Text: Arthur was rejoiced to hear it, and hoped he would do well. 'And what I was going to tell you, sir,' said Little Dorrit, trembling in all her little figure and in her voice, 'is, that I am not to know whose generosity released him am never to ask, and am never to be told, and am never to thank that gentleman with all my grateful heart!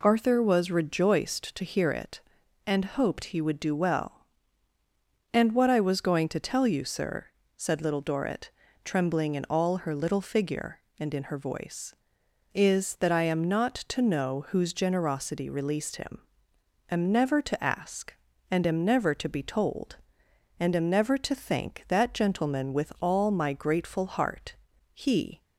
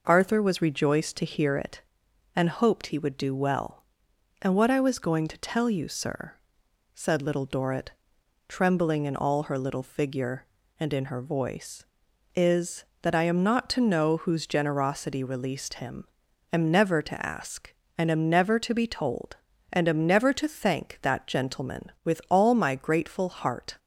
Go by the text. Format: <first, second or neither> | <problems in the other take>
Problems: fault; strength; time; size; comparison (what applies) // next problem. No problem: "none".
second | pauses between "him" and "am"; noticeable; at 16.2 s; 0.68 s long; noticeable in the second // goes on to say "He"; slight; from 24.9 s on; 0.48 s long